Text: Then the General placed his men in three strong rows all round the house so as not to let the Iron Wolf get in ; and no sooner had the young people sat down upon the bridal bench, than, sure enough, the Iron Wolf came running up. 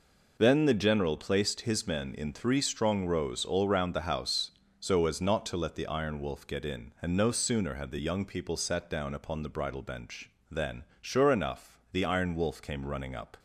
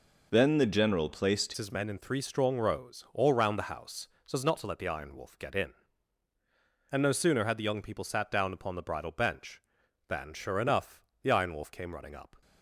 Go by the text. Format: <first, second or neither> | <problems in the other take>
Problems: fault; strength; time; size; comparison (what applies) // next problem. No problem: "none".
first | changes voice at "his"; from 1.5 s on; 10.9 s long